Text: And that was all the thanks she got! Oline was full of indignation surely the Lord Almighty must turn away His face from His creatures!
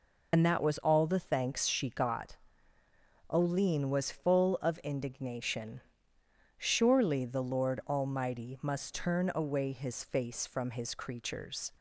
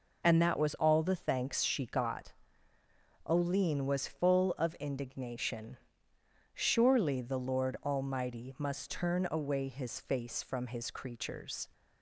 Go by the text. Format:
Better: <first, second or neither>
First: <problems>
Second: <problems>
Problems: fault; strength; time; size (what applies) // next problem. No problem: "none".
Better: second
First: loses the start of "And"; at 0.3 s; 55 ms // pauses between "indignation" and "surely"; noticeable; at 5.7 s; 0.78 s long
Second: pauses between "indignation" and "surely"; noticeable; at 5.7 s; 0.78 s long